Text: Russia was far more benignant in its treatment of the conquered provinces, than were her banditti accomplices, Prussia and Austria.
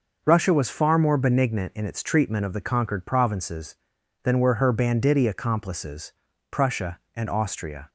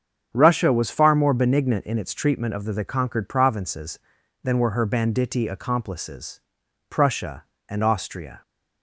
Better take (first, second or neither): first